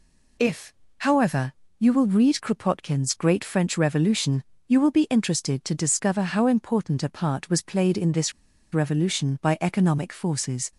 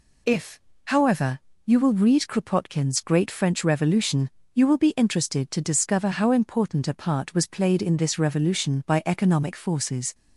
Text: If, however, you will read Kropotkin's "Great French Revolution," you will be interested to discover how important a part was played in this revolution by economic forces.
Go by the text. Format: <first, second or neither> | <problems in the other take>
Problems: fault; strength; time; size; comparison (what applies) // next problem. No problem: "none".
second | pauses between "this" and "revolution"; at 8.3 s; 0.41 s long